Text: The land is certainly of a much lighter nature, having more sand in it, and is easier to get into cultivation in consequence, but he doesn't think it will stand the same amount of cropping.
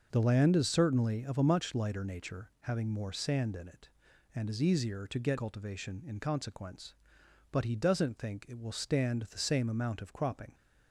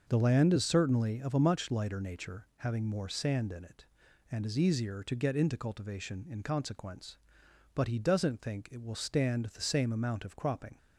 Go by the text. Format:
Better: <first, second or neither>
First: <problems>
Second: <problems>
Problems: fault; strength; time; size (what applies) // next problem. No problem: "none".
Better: second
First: starts louder than the rest; noticeable; until 1.1 s; 6 dB // skips "into"; at 5.3 s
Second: none